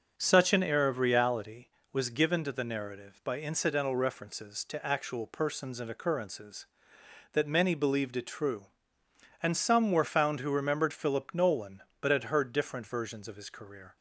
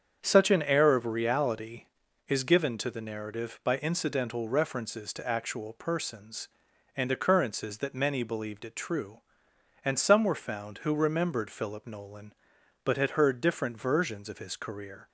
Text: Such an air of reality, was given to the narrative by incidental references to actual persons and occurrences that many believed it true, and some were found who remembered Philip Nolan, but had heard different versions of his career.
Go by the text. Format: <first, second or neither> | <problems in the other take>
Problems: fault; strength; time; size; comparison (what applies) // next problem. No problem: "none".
first | starts louder than the rest; strong; until 1.2 s; 7.5 dB; also in the first // says "is" for "was"; at 2.2 s